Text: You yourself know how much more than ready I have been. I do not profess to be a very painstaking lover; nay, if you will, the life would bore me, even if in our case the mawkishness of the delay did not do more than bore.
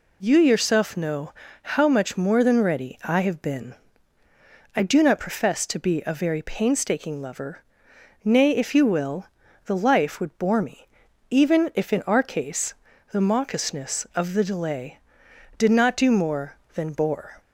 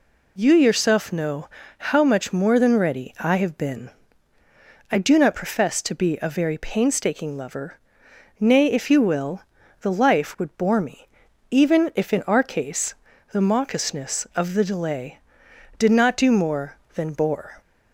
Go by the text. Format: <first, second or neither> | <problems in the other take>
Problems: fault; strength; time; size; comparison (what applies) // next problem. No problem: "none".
neither | pauses between "know" and "how"; slight; the same in both // pauses between "case" and "the"; the same in both